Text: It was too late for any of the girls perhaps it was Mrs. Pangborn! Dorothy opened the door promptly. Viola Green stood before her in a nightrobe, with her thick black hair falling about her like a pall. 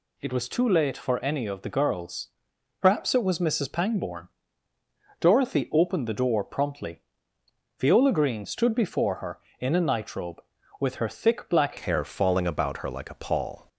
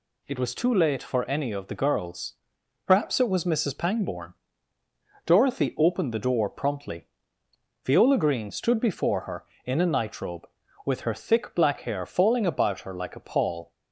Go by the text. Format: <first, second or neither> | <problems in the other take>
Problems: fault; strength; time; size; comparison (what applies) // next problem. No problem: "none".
second | pauses between "girls" and "perhaps"; noticeable; at 2.2 s; 0.52 s long; noticeable in the second // changes voice at "hair"; from 11.7 s on; 1.9 s long